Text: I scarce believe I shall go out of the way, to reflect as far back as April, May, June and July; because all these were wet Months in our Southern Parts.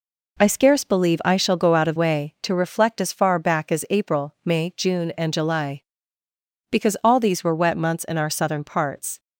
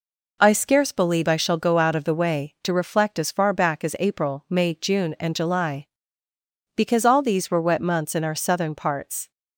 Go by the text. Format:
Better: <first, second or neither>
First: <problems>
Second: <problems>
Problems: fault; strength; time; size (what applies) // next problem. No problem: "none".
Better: second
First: skips "the"; at 1.9 s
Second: none